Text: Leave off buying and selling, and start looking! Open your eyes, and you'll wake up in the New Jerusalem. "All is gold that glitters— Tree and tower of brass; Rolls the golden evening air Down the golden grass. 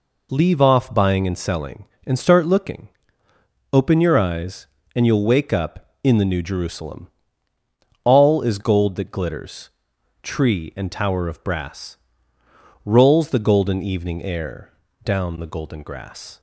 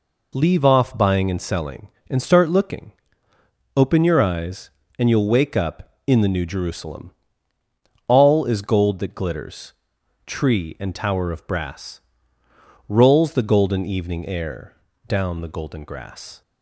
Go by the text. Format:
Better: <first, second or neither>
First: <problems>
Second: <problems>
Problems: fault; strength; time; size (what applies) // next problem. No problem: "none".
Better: neither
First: pauses between "air" and "Down"; slight; at 14.7 s; 0.32 s long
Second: pauses between "air" and "Down"; slight; at 14.7 s; 0.32 s long